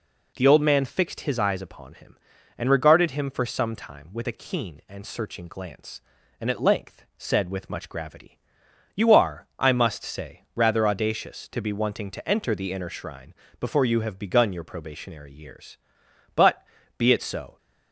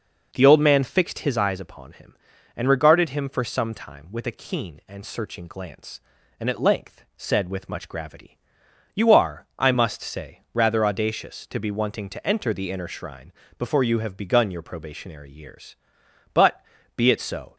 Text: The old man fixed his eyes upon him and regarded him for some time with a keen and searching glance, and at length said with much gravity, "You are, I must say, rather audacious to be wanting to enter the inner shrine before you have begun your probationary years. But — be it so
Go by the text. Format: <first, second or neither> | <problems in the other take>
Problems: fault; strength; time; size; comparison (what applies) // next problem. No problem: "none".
first | starts louder than the rest; noticeable; until 1.5 s; 5.5 dB // pauses between "shrine" and "before"; slight; at 13.3 s; 0.26 s long; slight in the first